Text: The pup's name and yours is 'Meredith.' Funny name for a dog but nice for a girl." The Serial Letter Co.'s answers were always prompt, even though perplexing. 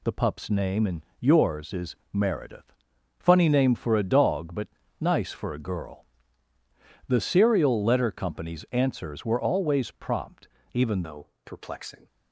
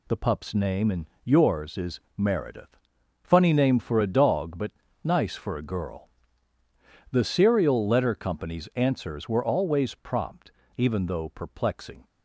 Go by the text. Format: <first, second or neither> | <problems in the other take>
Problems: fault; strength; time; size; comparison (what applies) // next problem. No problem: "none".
second | pauses between "and" and "yours"; slight; at 1.0 s; 0.18 s long; slight in the second // pauses between "is" and "Meredith"; slight; at 1.9 s; 0.16 s long; slight in the second // pauses between "but" and "nice"; slight; at 4.6 s; 0.32 s long; slight in the second // changes voice at "though"; from 11.0 s on; 1.0 s long // pauses between "though" and "perplexing"; slight; at 11.2 s; 0.18 s long